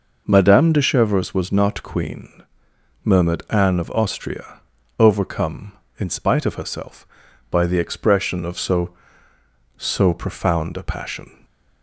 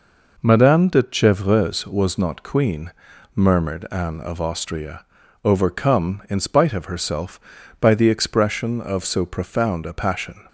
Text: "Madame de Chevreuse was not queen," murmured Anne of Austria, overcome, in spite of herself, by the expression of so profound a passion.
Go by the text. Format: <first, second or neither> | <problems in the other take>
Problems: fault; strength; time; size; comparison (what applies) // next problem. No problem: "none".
second | says "so" twice; at 9.7 s